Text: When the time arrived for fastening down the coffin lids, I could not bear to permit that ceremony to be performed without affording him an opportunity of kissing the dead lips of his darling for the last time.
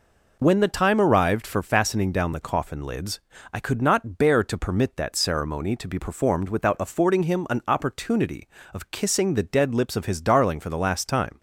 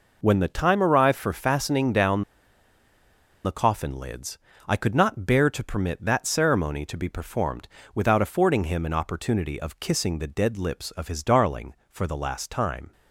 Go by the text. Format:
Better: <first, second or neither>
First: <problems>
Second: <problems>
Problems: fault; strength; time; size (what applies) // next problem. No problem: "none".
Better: first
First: none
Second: pauses between "down" and "the"; at 2.2 s; 1.2 s long // pauses between "performed" and "without"; slight; at 7.6 s; 0.28 s long